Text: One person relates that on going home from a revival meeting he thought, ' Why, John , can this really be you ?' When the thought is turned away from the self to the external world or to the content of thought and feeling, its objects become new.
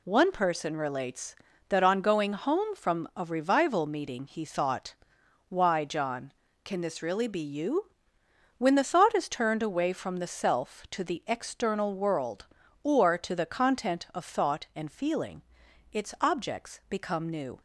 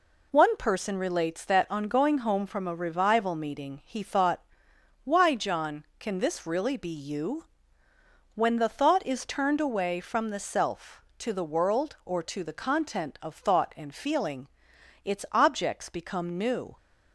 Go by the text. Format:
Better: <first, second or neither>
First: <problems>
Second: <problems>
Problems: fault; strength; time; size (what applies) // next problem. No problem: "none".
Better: first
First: none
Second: skips "external"; at 11.4 s